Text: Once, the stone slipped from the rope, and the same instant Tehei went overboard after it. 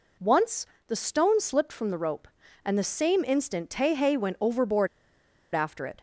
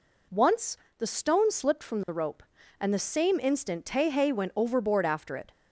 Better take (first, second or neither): second